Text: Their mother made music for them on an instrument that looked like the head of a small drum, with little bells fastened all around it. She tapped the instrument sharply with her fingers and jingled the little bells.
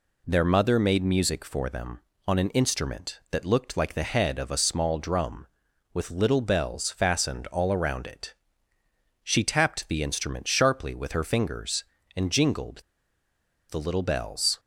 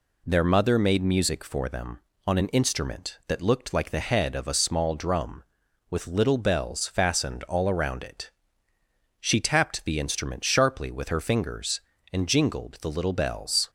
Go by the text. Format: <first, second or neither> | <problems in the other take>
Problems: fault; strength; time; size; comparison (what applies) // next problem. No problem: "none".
second | pauses between "jingled" and "the"; noticeable; at 12.8 s; 0.88 s long